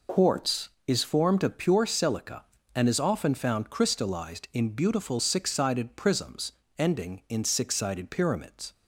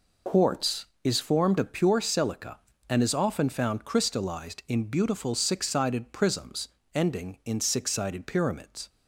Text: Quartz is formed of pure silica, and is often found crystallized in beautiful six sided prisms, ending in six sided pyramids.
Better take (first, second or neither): neither